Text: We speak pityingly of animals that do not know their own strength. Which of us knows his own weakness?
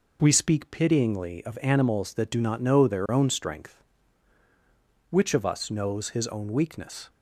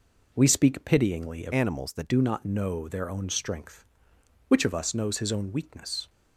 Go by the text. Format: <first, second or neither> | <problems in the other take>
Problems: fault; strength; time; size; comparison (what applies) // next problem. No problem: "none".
first | changes voice from "animals" to "that"; from 1.5 to 2.0 s; 0.5 s long